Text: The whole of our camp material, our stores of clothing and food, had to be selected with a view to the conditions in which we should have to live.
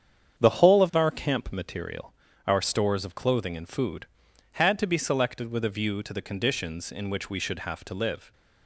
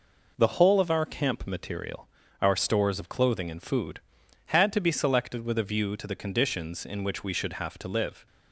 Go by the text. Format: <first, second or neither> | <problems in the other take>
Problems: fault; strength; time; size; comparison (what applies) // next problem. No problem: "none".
second | starts louder than the rest; strong; until 1.3 s; 8 dB